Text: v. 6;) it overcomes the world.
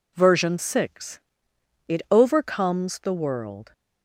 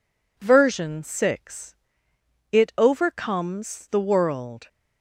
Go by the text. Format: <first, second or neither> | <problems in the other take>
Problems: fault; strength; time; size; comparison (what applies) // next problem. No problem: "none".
neither | none